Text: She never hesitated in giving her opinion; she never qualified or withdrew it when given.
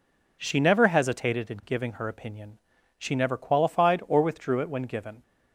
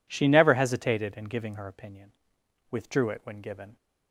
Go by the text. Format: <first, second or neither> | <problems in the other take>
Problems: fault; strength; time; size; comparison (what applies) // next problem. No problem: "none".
first | skips "she never qualified or"; at 2.4 s